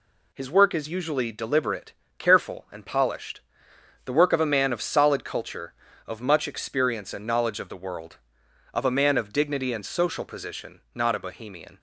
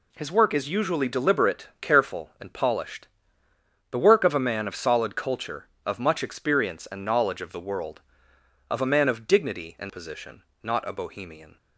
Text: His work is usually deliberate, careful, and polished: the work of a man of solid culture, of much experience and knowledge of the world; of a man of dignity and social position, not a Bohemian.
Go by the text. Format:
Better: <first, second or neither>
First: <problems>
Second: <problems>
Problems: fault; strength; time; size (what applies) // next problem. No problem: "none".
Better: first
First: none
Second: skips "social"; at 9.8 s